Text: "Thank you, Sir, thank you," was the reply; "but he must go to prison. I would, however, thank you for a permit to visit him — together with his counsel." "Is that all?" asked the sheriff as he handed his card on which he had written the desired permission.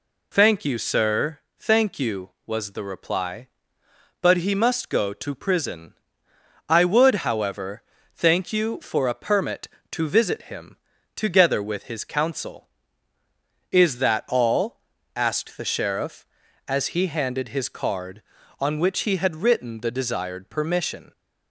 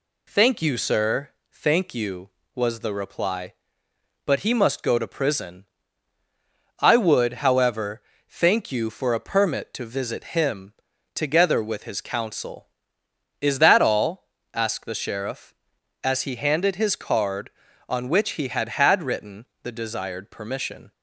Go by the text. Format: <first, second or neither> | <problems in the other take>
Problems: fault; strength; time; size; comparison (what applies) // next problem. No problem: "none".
first | says "had" twice; at 18.6 s // pauses between "written" and "the"; slight; at 19.4 s; 0.16 s long